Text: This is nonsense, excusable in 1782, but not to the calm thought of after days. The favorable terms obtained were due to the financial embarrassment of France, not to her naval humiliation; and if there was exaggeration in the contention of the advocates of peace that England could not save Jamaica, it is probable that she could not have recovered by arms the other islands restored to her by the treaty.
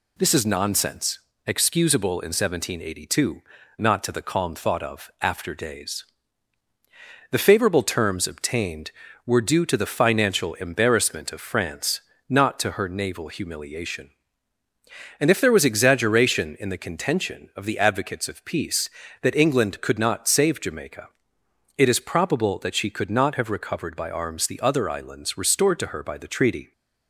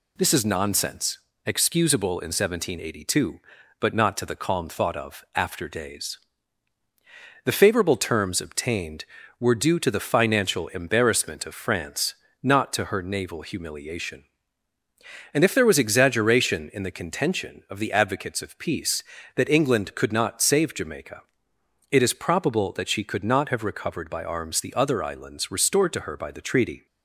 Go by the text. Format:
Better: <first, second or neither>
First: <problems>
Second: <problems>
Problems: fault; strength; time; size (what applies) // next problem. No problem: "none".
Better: second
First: skips "but"; at 3.6 s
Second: none